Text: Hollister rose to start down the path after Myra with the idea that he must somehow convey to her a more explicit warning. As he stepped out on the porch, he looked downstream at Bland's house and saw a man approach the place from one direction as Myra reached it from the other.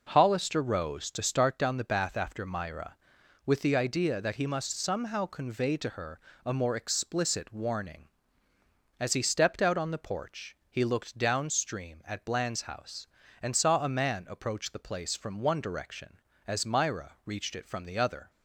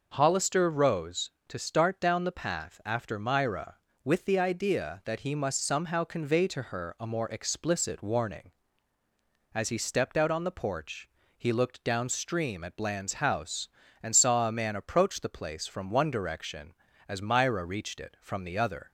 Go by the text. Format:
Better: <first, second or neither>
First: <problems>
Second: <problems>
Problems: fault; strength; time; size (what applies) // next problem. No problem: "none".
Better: second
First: says "bath" for "path"; at 1.8 s // pauses between "her" and "a"; slight; at 6.1 s; 0.24 s long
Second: none